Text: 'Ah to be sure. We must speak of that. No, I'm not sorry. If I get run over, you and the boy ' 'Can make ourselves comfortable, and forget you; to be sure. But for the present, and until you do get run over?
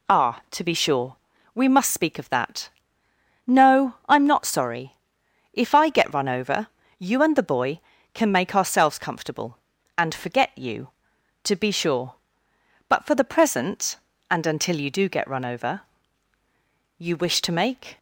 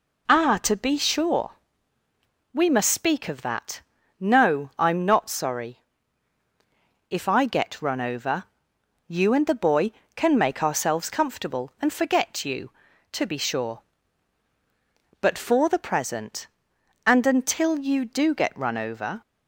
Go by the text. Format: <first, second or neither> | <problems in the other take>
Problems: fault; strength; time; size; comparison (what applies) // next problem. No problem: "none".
second | goes on to say "You wish to make"; noticeable; from 16.9 s on; 1.0 s long